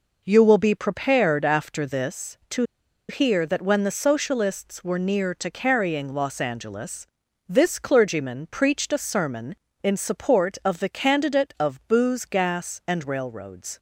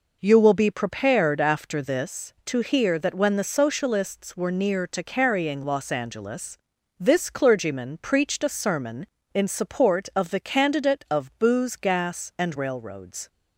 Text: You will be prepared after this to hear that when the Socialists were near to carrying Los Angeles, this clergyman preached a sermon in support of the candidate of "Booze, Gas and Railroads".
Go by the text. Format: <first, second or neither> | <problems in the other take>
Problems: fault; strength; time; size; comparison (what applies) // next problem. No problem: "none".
second | pauses between "to" and "hear"; noticeable; at 2.6 s; 0.46 s long